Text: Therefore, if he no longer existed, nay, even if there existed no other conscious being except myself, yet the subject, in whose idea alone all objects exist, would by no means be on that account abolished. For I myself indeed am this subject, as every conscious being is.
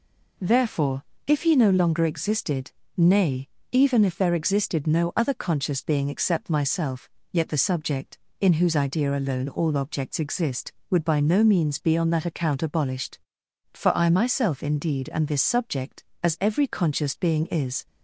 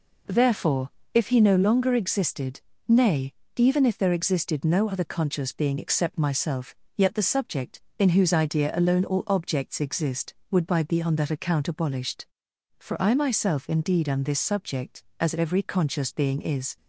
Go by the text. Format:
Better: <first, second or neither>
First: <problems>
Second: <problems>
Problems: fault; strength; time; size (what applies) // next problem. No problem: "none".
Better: first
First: none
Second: skips "no means"; at 10.8 s